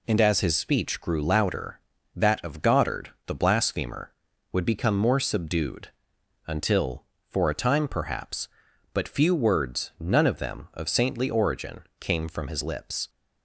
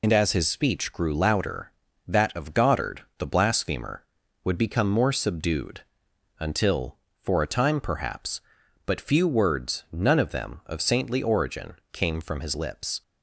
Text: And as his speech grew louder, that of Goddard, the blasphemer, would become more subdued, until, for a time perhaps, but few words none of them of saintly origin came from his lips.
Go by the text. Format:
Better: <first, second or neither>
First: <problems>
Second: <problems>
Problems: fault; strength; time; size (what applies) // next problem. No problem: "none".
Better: first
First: pauses between "origin" and "came"; slight; at 11.8 s; 0.18 s long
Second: loses the start of "And"; at 0.0 s; 45 ms // pauses between "origin" and "came"; slight; at 11.7 s; 0.18 s long